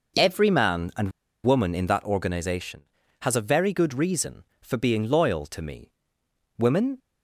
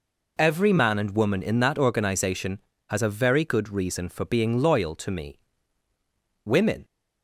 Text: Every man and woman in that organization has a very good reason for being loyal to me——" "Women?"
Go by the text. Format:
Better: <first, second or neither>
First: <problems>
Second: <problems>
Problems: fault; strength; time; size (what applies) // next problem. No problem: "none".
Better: second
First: pauses between "and" and "woman"; slight; at 1.0 s; 0.34 s long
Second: none